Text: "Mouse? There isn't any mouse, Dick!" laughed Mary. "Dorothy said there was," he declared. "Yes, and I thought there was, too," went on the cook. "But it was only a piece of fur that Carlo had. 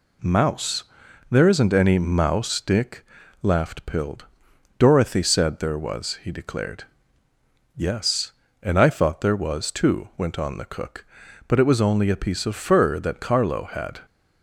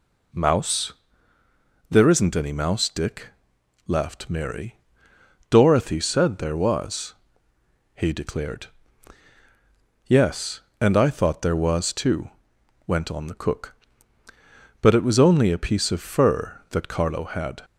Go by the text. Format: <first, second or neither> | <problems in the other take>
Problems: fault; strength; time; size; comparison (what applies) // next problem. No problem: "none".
second | says "Pild" for "Mary"; at 3.8 s